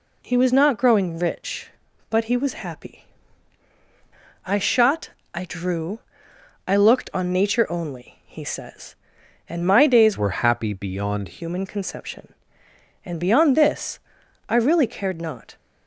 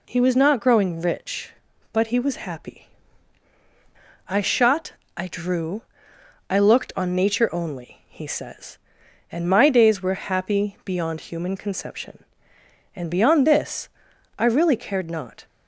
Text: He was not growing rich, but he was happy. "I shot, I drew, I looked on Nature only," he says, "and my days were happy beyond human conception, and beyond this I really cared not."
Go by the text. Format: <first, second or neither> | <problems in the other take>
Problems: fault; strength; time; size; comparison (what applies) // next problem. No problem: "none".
second | changes voice from "were" to "beyond"; from 10.1 to 11.3 s; 1.2 s long // pauses between "this" and "I"; noticeable; at 13.9 s; 0.50 s long; noticeable in the second